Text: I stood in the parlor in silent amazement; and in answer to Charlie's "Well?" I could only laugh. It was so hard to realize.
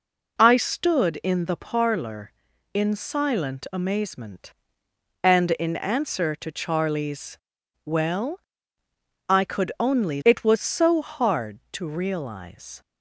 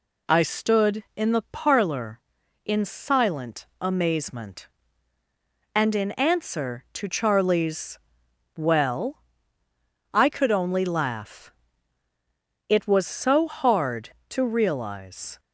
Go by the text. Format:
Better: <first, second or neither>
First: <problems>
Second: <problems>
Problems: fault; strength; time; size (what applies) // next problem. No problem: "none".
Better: second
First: pauses between "Charlie's" and "Well"; noticeable; at 7.3 s; 0.48 s long // skips "laugh"; at 10.2 s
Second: pauses between "Charlie's" and "Well"; noticeable; at 7.9 s; 0.58 s long